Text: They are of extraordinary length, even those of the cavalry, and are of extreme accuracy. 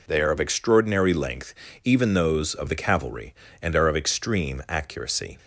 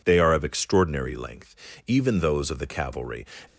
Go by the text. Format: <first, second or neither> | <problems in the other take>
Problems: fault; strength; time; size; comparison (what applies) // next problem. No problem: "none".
first | stops before "and are of extreme accuracy"; at 3.4 s